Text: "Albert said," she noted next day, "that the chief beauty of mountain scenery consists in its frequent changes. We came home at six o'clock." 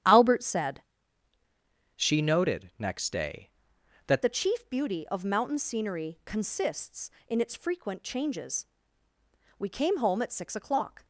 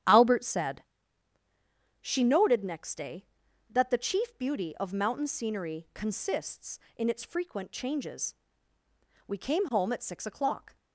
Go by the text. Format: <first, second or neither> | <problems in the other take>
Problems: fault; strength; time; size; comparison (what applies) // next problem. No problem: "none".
second | starts louder than the rest; strong; until 2.1 s; 10 dB; strong in the second // changes voice from "she" to "that"; from 1.9 to 4.2 s; 2.3 s long